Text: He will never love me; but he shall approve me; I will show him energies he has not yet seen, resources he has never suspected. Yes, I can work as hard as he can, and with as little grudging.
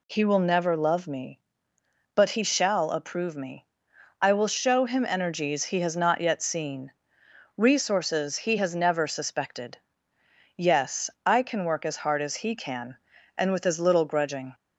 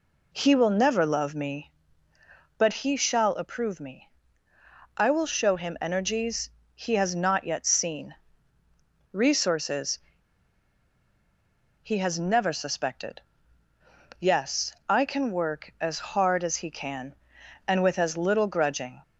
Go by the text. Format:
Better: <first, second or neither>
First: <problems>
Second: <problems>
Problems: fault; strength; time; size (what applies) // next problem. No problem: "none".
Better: first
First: none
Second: pauses between "energies" and "he"; slight; at 6.4 s; 0.24 s long // pauses between "resources" and "he"; strong; at 9.9 s; 1.8 s long